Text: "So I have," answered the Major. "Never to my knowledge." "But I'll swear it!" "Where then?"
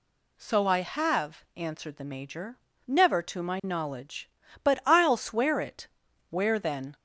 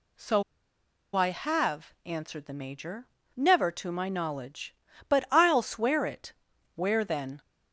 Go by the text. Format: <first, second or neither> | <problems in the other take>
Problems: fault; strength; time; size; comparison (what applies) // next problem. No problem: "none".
first | pauses between "So" and "I"; noticeable; at 0.4 s; 0.73 s long